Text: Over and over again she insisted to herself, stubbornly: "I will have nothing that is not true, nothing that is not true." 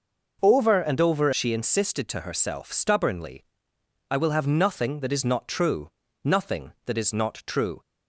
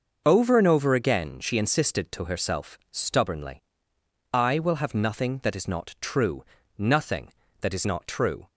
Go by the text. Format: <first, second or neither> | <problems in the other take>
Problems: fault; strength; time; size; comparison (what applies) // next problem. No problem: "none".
second | skips "again"; at 1.3 s